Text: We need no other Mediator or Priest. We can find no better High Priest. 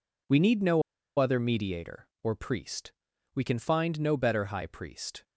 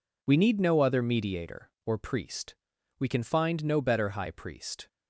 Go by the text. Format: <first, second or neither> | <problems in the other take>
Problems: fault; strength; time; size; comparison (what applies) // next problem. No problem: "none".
second | pauses between "no" and "other"; at 0.8 s; 0.37 s long